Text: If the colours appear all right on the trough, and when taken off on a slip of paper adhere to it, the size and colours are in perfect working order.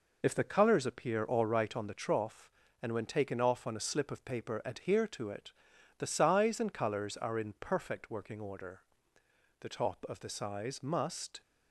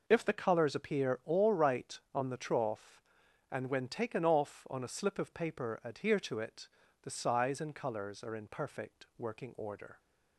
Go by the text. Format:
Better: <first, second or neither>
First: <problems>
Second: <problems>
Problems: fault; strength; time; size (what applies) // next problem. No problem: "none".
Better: second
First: goes on to say "The top of the size must"; strong; from 9.6 s on; 1.8 s long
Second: none